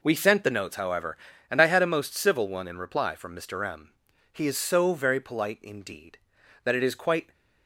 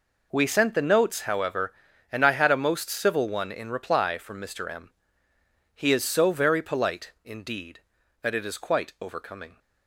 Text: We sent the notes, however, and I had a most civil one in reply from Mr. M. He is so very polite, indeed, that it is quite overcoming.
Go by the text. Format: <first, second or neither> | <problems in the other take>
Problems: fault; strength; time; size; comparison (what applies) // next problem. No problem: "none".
second | stops before "overcoming"; at 7.3 s